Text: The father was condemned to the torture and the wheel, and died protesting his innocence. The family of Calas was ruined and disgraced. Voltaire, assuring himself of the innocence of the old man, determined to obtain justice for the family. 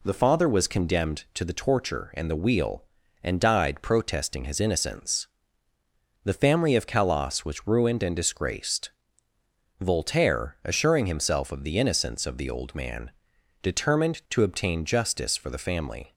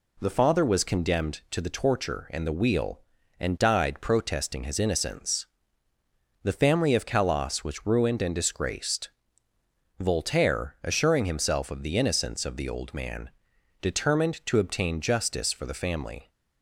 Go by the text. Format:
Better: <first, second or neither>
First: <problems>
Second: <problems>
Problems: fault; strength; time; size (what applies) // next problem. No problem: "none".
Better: neither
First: none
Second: none